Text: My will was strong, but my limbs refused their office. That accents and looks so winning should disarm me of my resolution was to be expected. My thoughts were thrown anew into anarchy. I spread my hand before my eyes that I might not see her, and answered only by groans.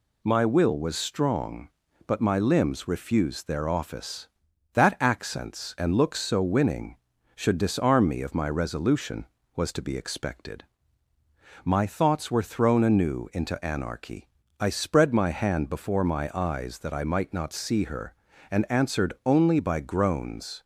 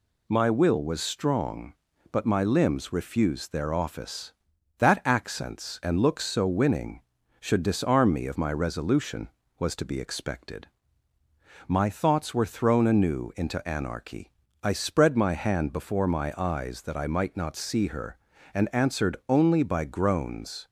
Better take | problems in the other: neither | none

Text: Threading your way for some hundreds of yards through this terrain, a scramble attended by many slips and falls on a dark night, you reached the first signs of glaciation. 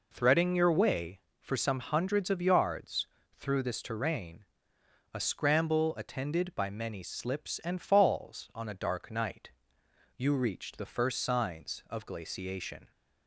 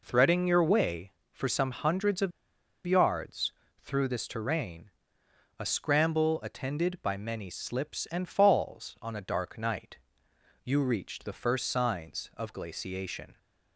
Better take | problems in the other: first | pauses between "of" and "yards"; noticeable; at 2.3 s; 0.56 s long // pauses between "yards" and "through"; slight; at 3.5 s; 0.32 s long; slight in the first

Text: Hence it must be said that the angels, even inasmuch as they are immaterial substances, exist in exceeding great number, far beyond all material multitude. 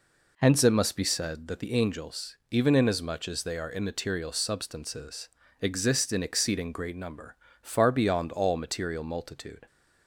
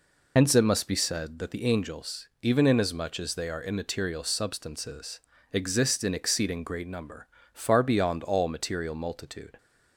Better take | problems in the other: first | loses the start of "Hence"; at 0.3 s; 85 ms

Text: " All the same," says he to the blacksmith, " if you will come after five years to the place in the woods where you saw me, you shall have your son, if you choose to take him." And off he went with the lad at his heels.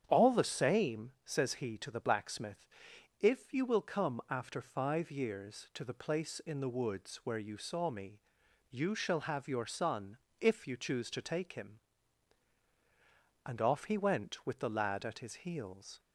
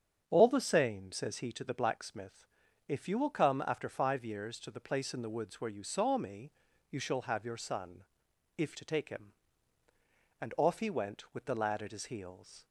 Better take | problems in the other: first | starts louder than the rest; strong; until 1.2 s; 8 dB; strong in the first // skips "you choose"; at 8.7 s

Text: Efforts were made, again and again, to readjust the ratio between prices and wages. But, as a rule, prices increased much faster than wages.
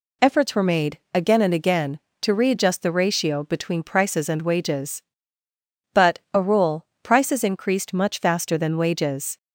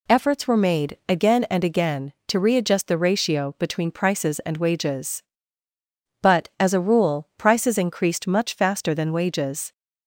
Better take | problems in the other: second | skips "as"; at 6.2 s

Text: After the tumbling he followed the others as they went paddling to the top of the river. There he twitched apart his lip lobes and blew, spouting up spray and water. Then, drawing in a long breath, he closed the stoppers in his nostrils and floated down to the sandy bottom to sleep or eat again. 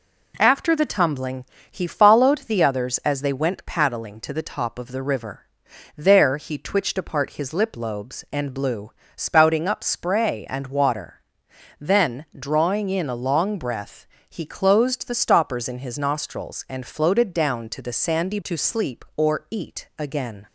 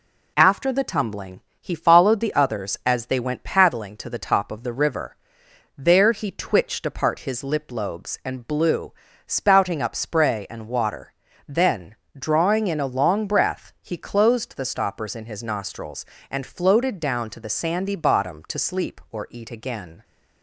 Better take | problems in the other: second | pauses between "tumbling" and "he"; slight; at 1.4 s; 0.26 s long; slight in the second // skips "bottom"; at 18.4 s

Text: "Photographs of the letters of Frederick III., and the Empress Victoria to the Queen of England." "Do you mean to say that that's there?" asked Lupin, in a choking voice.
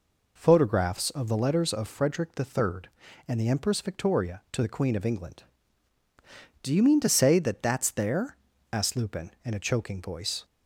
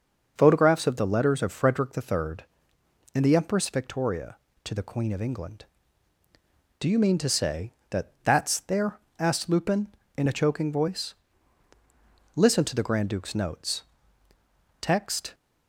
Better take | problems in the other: first | goes on to say "Listen to the grand duke's notes Text"; strong; from 12.3 s on; 3.0 s long

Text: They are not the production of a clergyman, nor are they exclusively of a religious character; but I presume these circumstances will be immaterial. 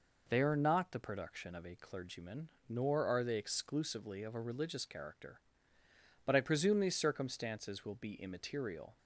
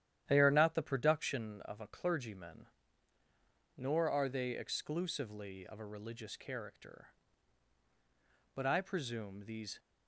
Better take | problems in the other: first | starts louder than the rest; strong; until 1.2 s; 11 dB // stops before "circumstances will be immaterial"; at 9.7 s

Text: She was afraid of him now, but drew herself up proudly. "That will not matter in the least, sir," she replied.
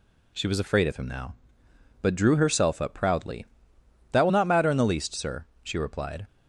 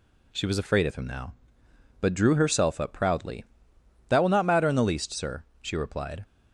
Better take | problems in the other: neither | none

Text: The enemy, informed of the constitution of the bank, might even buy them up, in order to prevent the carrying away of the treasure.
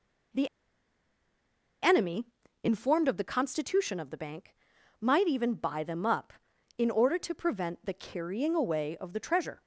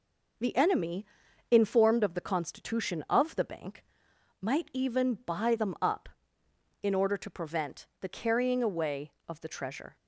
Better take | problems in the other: second | pauses between "The" and "enemy"; strong; at 0.4 s; 1.3 s long

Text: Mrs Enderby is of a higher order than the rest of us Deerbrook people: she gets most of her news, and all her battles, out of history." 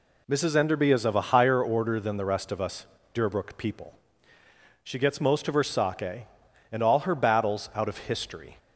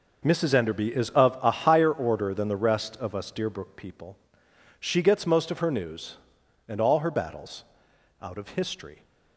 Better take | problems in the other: second | pauses between "us" and "Deerbrook"; slight; at 2.8 s; 0.26 s long // says "sake" for "news"; at 5.6 s

